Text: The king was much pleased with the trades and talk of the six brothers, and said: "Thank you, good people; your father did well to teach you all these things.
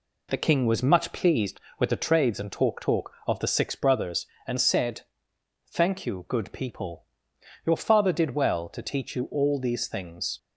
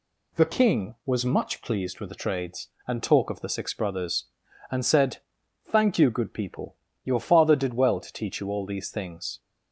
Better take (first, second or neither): second